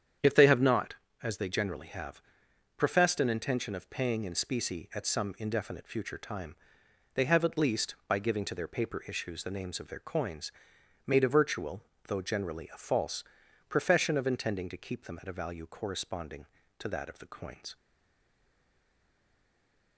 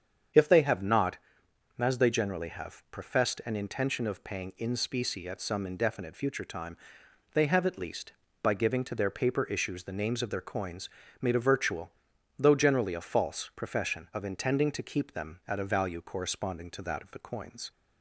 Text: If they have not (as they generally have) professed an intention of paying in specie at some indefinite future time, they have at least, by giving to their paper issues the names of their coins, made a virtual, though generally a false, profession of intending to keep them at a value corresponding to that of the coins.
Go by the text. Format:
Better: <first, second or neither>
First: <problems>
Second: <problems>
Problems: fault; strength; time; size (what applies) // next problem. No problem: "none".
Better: second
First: starts louder than the rest; strong; until 1.5 s; 8.5 dB // stays silent after the last word; from 17.7 s on; 2.2 s long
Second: starts louder than the rest; strong; until 1.9 s; 7.5 dB